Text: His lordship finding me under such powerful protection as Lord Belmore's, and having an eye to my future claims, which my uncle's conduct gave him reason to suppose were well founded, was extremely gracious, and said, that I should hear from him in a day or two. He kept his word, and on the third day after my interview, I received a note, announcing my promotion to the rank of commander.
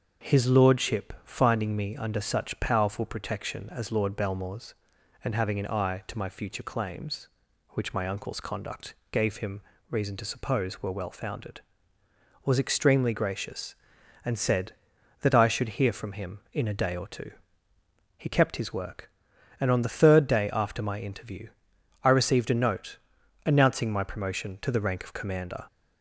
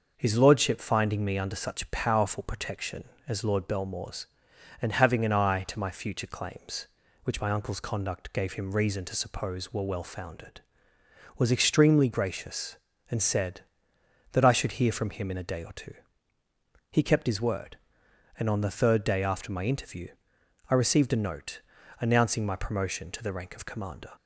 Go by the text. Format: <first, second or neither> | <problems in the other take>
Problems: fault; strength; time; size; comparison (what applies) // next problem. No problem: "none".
second | starts louder than the rest; until 1.3 s; 6.5 dB; noticeable in the second // pauses between "conduct" and "gave"; slight; at 8.9 s; 0.16 s long // pauses between "him" and "reason"; slight; at 9.6 s; 0.28 s long // says "work" for "word"; at 18.7 s